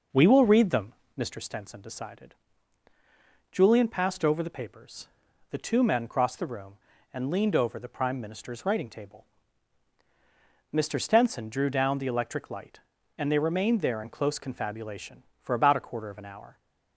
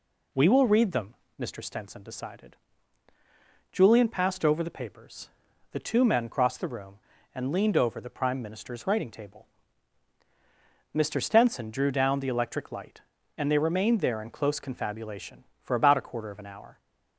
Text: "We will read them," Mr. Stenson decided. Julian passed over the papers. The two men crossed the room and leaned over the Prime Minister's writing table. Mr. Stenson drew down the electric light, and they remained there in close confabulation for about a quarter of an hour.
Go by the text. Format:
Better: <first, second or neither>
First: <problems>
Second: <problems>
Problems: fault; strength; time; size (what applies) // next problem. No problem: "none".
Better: second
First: starts louder than the rest; noticeable; until 1.4 s; 5.5 dB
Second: none